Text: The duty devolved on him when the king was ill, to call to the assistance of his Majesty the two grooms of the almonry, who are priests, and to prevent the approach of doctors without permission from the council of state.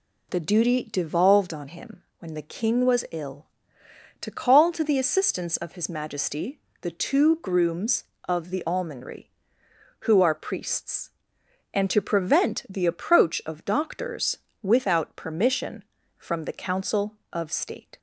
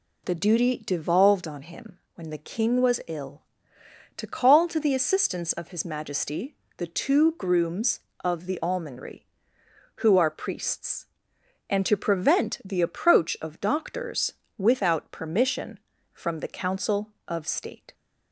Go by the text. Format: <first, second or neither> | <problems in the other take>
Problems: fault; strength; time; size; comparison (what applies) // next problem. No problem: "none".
neither | pauses between "him" and "when"; slight; the same in both // pauses between "Majesty" and "the"; slight; the same in both // pauses between "doctors" and "without"; slight; the same in both